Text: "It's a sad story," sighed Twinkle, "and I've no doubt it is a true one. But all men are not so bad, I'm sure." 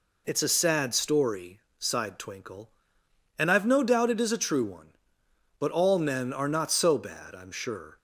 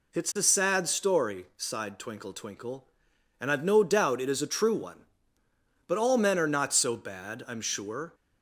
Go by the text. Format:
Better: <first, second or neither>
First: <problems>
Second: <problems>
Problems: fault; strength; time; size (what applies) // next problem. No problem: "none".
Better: first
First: none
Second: says "Twinkle" twice; at 2.3 s